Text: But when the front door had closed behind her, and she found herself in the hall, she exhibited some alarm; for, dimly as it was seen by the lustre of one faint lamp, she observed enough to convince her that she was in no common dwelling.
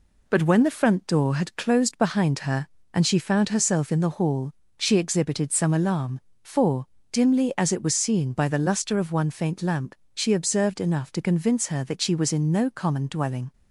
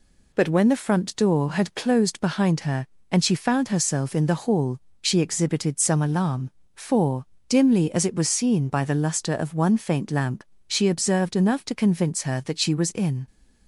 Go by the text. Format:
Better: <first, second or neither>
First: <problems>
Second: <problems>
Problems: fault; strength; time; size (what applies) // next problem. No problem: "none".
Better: first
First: none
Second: stops before "no common dwelling"; at 13.2 s